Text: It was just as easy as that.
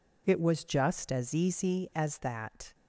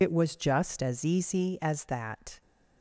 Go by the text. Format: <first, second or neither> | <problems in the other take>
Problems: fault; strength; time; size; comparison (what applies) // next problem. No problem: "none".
first | loses the start of "It"; at 0.0 s; 40 ms